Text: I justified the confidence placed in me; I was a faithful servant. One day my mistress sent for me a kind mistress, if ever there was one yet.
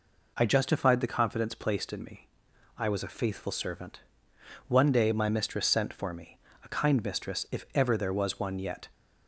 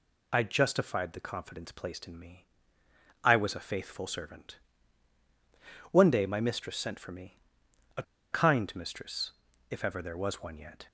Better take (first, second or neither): first